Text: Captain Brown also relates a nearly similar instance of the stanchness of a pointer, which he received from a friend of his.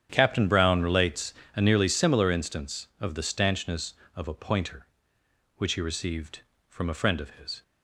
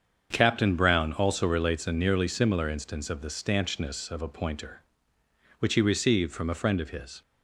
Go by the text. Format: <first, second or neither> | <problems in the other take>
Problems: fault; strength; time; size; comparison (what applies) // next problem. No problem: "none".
second | starts louder than the rest; strong; until 1.1 s; 9 dB; strong in the second // skips "also"; at 0.8 s // pauses between "relates" and "a"; slight; at 1.3 s; 0.22 s long